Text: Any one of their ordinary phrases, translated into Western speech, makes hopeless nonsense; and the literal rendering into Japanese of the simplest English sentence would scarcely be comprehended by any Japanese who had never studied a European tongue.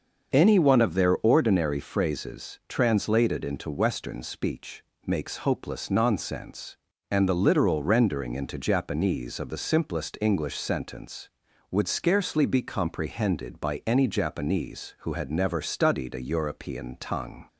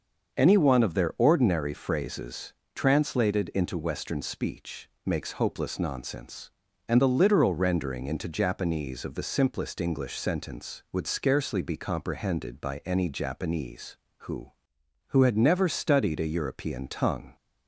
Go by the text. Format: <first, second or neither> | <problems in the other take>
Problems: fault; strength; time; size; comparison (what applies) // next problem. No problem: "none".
first | starts louder than the rest; until 1.4 s; 6.5 dB; also in the first // says "who" twice; at 15.0 s